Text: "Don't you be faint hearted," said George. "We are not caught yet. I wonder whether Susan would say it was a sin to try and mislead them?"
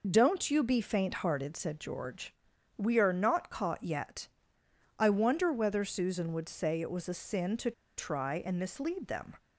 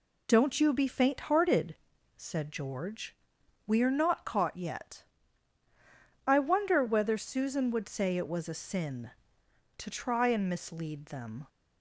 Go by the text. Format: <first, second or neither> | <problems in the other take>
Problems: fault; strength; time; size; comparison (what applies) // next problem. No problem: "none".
second | pauses between "to" and "try"; slight; at 7.7 s; 0.25 s long